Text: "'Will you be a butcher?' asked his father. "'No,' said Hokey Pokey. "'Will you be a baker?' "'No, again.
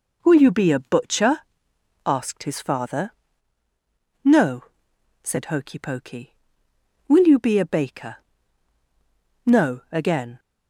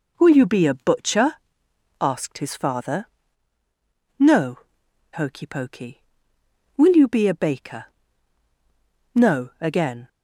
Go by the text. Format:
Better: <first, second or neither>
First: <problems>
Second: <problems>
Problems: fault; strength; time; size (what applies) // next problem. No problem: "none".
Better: first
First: none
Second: skips "said"; at 4.8 s